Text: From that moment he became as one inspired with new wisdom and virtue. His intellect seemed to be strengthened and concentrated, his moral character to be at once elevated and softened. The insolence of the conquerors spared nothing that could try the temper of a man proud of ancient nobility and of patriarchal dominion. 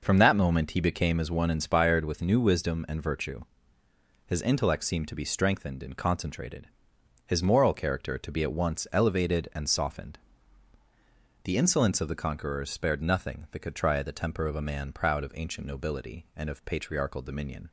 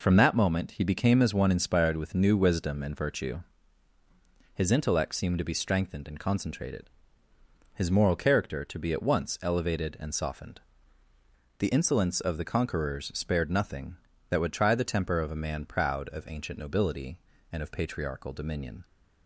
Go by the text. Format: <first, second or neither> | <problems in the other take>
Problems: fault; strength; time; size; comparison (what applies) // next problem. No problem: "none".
first | says "would" for "could"; at 14.4 s